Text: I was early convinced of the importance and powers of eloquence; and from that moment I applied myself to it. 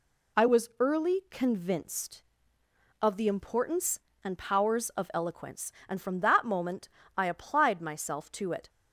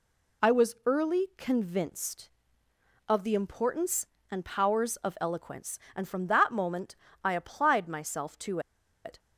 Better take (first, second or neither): first